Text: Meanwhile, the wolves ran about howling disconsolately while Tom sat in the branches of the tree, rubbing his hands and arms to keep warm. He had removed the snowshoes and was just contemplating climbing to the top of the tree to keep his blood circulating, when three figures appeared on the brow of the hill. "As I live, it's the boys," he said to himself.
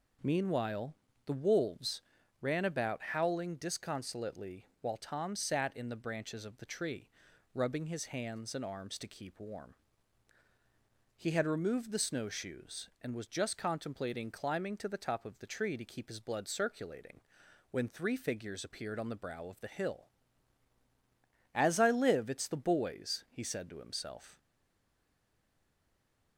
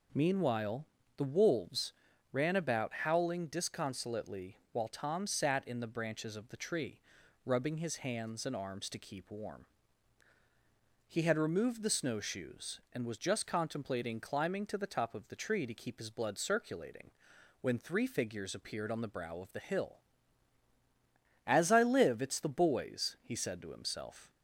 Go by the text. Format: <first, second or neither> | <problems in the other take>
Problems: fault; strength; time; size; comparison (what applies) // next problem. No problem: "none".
second | pauses between "wolves" and "ran"; at 2.0 s; 0.40 s long; also in the second // pauses between "disconsolately" and "while"; slight; at 4.6 s; 0.16 s long; slight in the second // stays silent after the last word; noticeable; from 24.3 s on; 2.0 s long